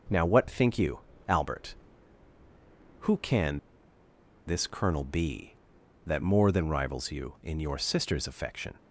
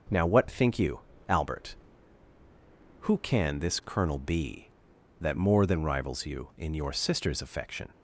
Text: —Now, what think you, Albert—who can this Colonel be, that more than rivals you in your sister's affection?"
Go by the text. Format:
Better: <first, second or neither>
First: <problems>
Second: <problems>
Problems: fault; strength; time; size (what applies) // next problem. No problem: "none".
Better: second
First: pauses between "can" and "this"; noticeable; at 3.5 s; 0.87 s long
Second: none